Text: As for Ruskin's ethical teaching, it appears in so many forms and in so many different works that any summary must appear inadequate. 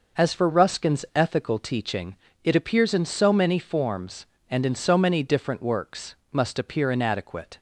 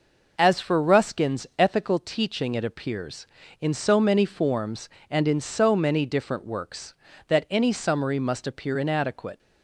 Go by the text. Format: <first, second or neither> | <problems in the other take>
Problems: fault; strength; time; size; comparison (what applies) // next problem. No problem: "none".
second | skips "that any summary"; at 6.2 s